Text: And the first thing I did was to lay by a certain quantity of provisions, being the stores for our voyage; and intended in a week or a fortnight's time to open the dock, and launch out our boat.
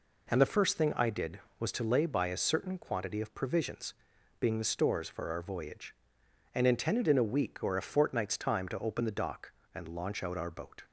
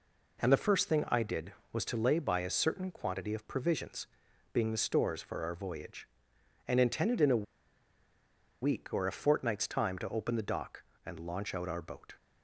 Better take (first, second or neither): first